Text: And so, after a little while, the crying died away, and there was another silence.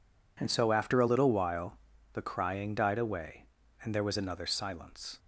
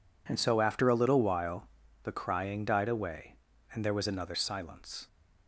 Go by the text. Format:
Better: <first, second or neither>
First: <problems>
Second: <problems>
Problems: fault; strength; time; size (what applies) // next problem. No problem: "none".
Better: neither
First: none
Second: none